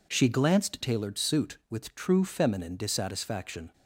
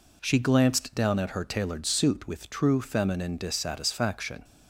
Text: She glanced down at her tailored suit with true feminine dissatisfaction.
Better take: second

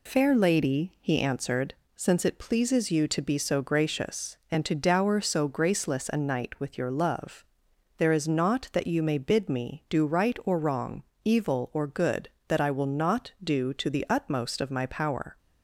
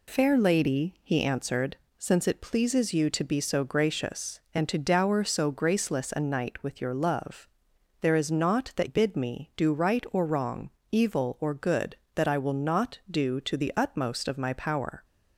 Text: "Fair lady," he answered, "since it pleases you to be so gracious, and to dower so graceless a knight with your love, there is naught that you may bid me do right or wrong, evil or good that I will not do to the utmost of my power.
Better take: first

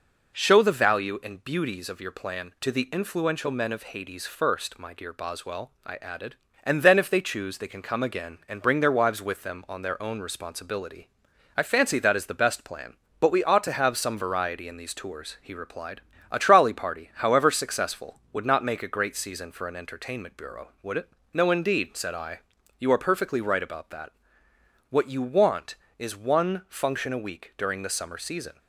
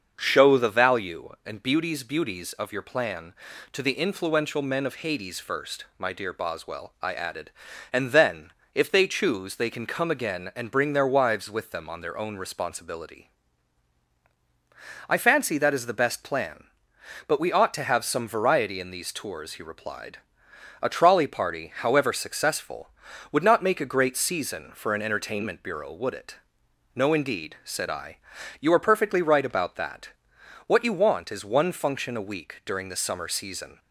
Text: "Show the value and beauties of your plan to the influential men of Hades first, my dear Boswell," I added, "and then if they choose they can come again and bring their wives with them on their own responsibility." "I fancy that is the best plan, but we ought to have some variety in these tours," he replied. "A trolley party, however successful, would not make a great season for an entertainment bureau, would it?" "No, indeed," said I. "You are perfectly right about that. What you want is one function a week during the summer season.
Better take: first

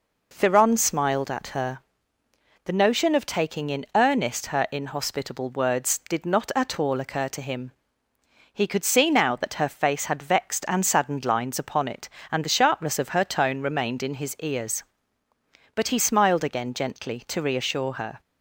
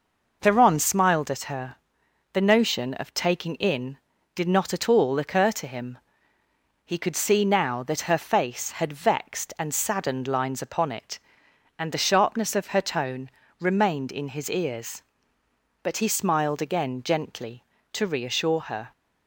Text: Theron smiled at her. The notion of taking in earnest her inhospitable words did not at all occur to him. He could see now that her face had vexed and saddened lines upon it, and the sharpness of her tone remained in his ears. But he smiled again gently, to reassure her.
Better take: first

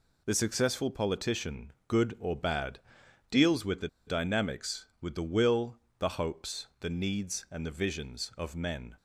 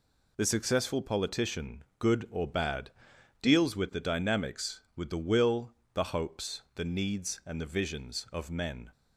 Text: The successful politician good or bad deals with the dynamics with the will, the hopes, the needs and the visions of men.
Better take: second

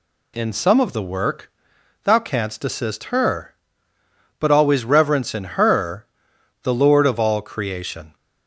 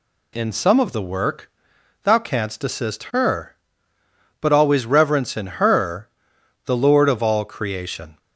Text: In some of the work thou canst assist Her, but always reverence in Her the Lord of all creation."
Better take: neither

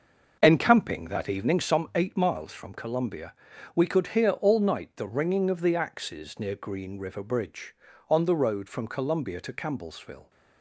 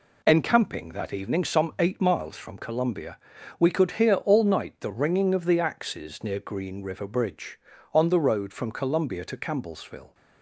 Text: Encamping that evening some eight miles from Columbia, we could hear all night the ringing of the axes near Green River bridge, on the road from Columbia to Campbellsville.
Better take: second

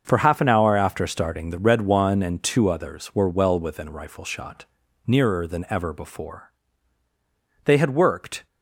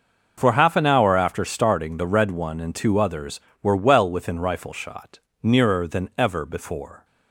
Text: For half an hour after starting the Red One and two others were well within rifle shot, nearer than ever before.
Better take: second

